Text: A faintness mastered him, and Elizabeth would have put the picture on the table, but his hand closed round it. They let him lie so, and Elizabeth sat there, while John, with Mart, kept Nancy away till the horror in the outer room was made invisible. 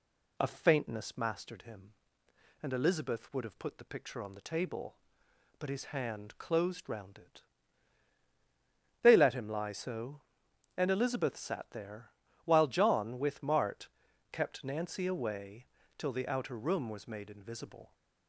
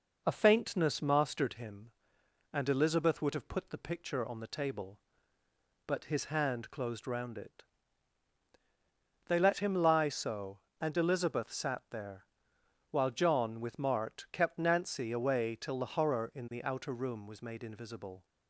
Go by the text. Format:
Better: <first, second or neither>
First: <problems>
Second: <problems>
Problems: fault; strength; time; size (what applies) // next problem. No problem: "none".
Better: second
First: pauses between "away" and "till"; slight; at 15.6 s; 0.32 s long // skips "the horror in"; at 16.1 s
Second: none